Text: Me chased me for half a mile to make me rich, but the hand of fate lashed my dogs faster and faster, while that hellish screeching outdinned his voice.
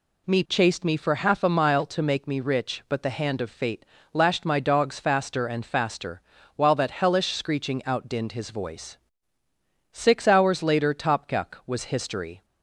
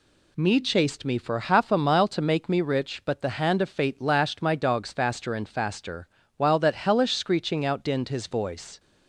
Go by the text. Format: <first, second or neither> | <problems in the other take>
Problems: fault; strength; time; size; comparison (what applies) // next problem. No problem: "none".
second | pauses between "fate" and "lashed"; slight; at 3.8 s; 0.28 s long // goes on to say "Six hours later Topkuk was history"; strong; from 9.9 s on; 2.5 s long